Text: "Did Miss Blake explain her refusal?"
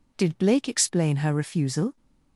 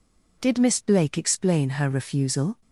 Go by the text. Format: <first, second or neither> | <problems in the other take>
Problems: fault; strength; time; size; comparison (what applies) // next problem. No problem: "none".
second | skips "Miss"; at 0.3 s